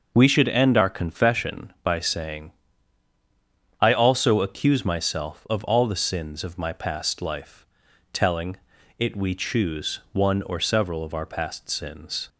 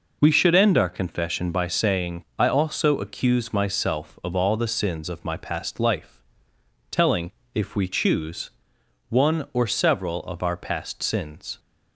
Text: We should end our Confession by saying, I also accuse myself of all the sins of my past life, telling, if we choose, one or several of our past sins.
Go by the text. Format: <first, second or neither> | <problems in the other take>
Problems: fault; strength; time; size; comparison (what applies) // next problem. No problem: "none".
second | starts louder than the rest; noticeable; until 1.1 s; 6 dB // says "it" for "if"; at 8.9 s